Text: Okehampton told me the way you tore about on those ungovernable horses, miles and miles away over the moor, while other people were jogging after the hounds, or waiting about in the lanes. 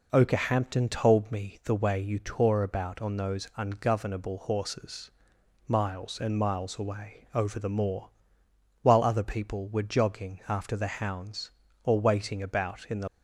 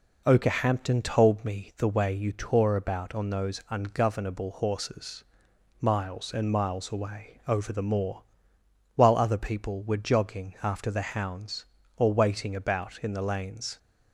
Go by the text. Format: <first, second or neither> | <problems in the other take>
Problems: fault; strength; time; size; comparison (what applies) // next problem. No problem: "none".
second | stops before "lanes"; at 13.0 s